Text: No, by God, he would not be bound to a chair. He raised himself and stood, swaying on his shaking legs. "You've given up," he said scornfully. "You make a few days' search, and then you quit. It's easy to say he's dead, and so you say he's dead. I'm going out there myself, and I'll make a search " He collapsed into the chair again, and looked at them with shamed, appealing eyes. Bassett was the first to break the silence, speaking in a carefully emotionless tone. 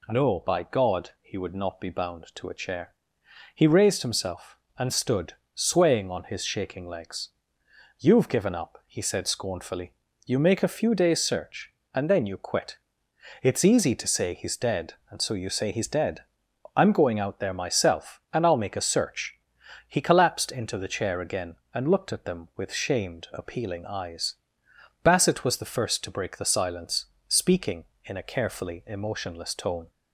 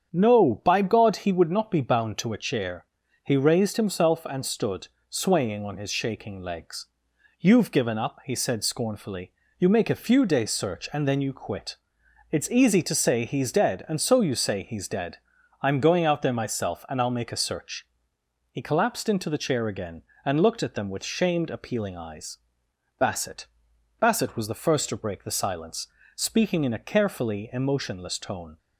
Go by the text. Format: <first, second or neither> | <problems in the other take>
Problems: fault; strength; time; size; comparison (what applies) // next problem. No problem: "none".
first | starts louder than the rest; strong; until 1.1 s; 8 dB // says "Bassett" twice; at 23.9 s